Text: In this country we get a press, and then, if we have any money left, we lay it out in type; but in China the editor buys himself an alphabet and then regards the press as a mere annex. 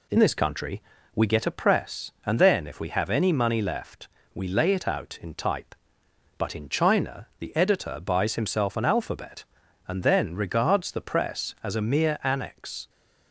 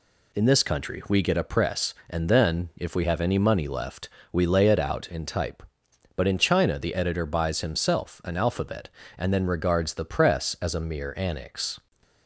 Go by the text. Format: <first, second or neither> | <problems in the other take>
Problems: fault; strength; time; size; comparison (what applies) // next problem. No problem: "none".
second | changes voice at "this"; from 0.1 s on; 12.7 s long // pauses between "country" and "we"; slight; at 0.8 s; 0.34 s long